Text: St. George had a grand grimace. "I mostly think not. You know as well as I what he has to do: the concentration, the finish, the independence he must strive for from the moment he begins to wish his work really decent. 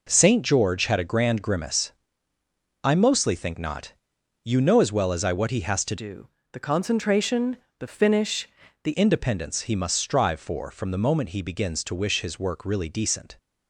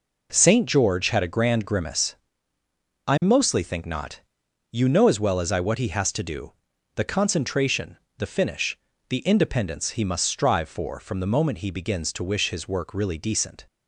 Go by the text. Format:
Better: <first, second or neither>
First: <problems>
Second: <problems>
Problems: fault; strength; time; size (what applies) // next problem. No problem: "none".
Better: second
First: changes voice from "do" to "the"; from 5.9 to 8.9 s; 3.0 s long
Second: none